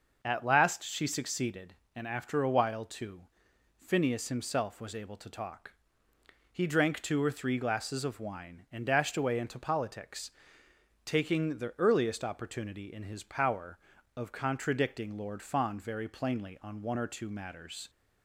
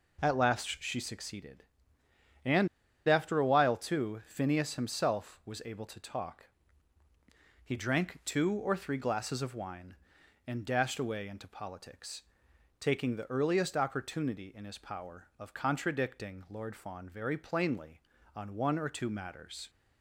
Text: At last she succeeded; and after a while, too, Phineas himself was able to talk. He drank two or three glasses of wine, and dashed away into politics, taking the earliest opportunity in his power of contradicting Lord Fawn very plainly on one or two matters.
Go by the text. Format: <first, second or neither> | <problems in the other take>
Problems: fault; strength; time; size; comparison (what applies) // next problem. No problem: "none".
first | pauses between "and" and "after"; at 2.6 s; 0.39 s long